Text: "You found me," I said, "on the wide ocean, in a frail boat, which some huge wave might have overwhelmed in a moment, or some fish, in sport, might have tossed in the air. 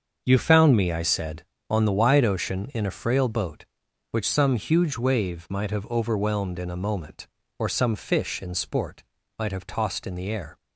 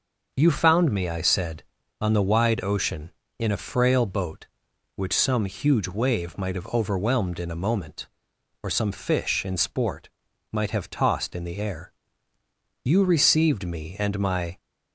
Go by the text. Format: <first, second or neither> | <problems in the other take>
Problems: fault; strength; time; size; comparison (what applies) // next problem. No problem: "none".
first | starts louder than the rest; until 1.3 s; 6 dB; also in the first // goes on to say "You received me and my"; strong; from 12.8 s on; 1.7 s long